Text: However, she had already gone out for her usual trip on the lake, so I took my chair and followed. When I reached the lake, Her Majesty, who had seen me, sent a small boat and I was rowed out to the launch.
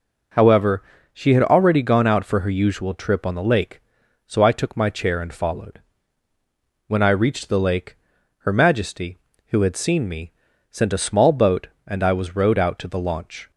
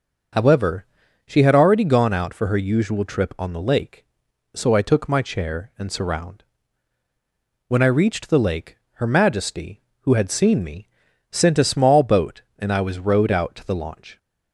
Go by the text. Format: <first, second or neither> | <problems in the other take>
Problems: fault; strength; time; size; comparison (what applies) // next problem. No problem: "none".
first | starts louder than the rest; noticeable; until 1.7 s; 6 dB // says "surround" for "followed"; at 5.9 s